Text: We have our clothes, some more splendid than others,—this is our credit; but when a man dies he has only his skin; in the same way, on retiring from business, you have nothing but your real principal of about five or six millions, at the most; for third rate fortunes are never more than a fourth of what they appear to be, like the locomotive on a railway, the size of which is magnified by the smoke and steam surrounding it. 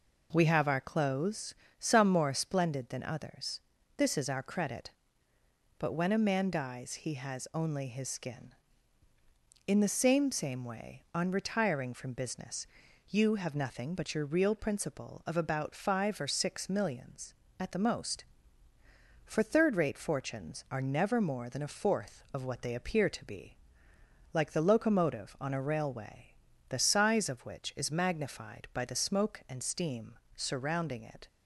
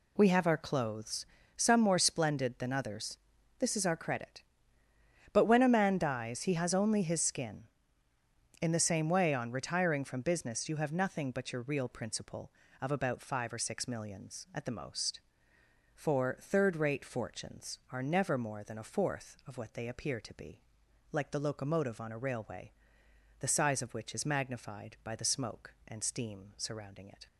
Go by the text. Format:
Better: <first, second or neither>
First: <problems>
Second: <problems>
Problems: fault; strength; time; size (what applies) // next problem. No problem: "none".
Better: second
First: says "same" twice; at 10.3 s // pauses between "steam" and "surrounding"; slight; at 30.1 s; 0.20 s long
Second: none